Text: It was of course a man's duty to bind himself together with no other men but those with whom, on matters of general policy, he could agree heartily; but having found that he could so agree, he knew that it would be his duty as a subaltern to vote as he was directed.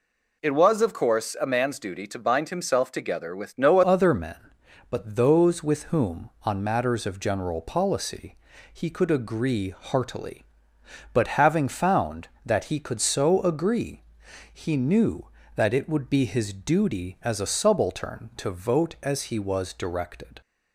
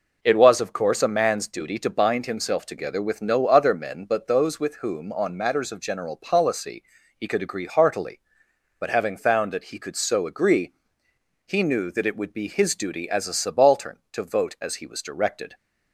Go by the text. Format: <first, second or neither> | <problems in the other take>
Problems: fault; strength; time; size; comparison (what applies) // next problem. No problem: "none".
second | changes voice at "other"; from 3.8 s on; 16.6 s long